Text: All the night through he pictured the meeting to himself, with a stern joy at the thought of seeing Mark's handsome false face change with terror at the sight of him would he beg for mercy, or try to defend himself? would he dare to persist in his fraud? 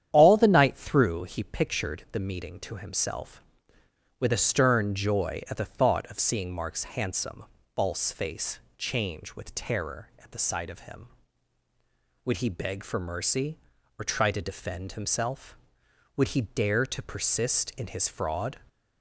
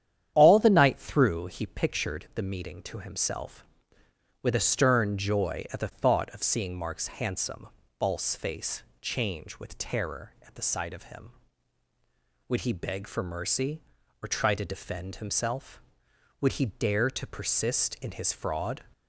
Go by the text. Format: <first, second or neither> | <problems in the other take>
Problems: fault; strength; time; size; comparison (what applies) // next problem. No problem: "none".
neither | starts louder than the rest; strong; the same in both // pauses between "handsome" and "false"; slight; the same in both // pauses between "face" and "change"; slight; the same in both